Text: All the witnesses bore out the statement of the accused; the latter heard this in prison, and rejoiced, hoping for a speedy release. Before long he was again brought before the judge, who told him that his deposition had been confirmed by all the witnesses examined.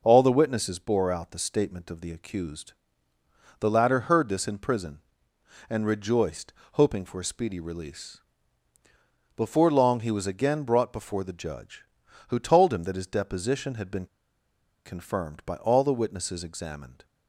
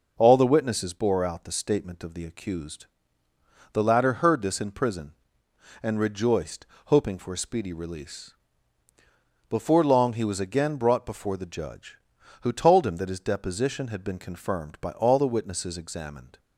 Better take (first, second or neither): second